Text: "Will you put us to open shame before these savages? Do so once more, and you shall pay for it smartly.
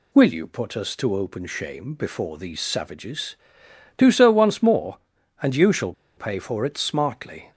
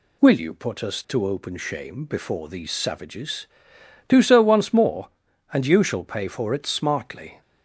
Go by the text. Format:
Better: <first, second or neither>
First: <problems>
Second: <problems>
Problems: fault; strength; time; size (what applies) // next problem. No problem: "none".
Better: second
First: pauses between "shall" and "pay"; slight; at 5.9 s; 0.22 s long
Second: none